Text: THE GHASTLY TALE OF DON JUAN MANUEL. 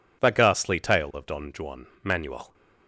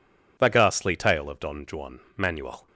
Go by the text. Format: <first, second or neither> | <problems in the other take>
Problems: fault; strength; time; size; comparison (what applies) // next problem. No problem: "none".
neither | pauses between "JUAN" and "MANUEL"; slight; the same in both